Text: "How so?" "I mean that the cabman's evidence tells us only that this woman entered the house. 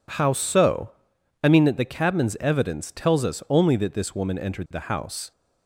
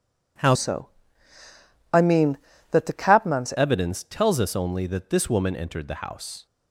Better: first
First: none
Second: changes voice from "so" to "cabman's"; from 0.5 to 3.5 s; 3.0 s long

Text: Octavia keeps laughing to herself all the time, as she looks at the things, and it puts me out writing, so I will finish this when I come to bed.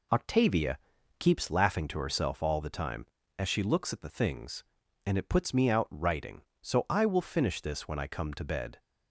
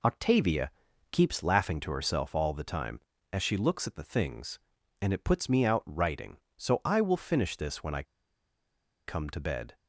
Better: first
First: pauses between "Octavia" and "keeps"; at 0.7 s; 0.42 s long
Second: pauses between "Octavia" and "keeps"; at 0.7 s; 0.42 s long // pauses between "I" and "come"; at 8.0 s; 1.0 s long

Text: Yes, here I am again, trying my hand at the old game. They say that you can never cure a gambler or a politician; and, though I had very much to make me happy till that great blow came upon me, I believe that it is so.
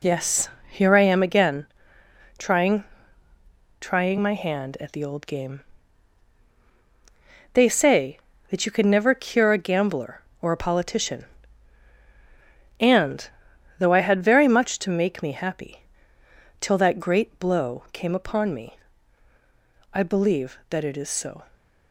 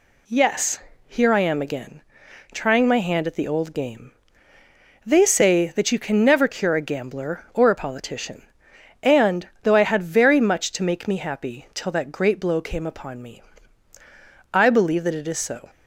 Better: second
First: says "trying" twice; at 3.7 s // pauses between "happy" and "till"; noticeable; at 15.8 s; 0.76 s long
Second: none

